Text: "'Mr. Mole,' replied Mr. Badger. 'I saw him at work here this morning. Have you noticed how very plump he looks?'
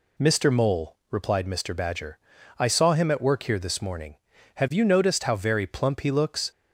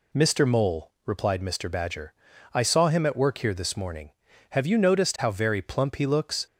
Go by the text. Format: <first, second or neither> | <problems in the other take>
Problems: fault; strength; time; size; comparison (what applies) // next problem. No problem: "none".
neither | none